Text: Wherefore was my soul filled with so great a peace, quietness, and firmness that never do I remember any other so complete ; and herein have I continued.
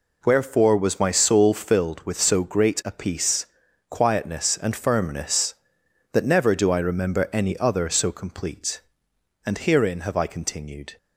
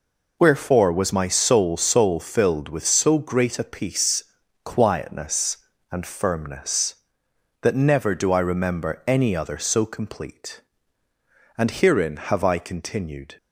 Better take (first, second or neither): first